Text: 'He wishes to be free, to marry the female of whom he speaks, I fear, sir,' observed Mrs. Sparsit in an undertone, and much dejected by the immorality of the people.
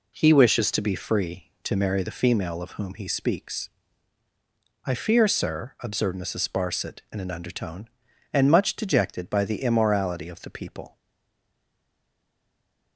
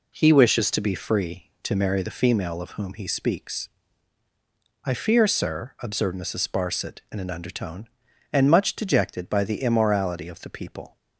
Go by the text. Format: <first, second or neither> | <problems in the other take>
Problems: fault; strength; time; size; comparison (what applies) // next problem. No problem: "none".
second | stays silent after the last word; noticeable; from 10.9 s on; 2.0 s long